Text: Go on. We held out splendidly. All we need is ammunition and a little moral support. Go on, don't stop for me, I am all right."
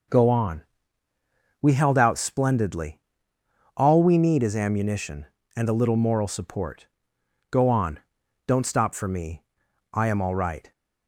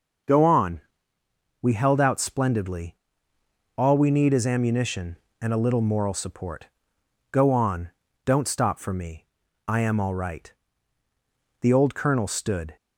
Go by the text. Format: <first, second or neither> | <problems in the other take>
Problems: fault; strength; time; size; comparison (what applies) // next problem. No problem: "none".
first | starts louder than the rest; until 2.0 s; 6.5 dB // goes on to say "The old colonel stood"; noticeable; from 11.5 s on; 1.1 s long